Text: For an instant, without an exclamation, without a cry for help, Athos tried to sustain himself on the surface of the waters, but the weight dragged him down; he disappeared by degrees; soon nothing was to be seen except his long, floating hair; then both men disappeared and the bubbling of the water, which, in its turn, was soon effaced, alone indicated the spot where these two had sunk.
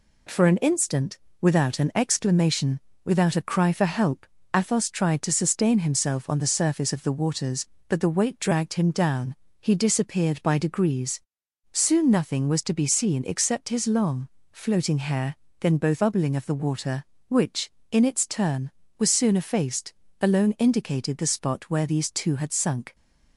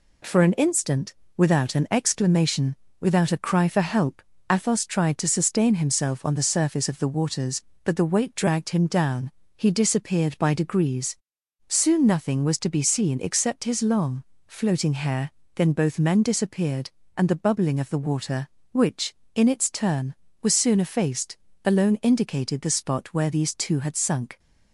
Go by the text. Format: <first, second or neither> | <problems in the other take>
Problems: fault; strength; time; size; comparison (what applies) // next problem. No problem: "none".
second | skips "men disappeared and the"; at 16.0 s